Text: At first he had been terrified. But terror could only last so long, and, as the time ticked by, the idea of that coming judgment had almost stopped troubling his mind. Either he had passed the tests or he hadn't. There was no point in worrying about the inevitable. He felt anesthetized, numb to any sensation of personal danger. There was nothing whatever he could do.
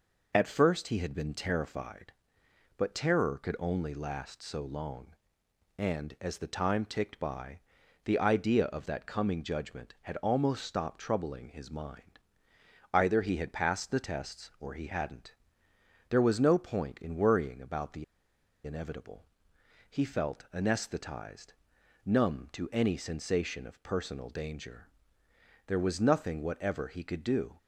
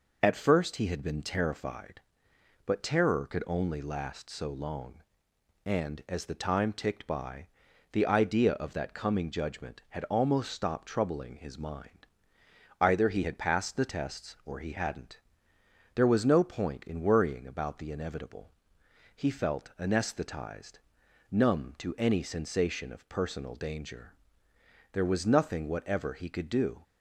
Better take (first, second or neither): second